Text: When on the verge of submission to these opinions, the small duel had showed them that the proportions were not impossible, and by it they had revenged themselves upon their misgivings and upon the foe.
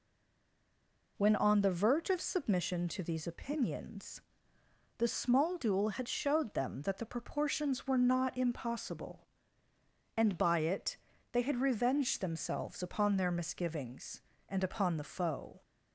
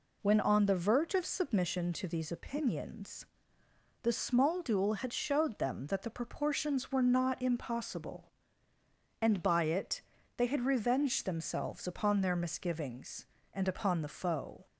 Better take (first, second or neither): second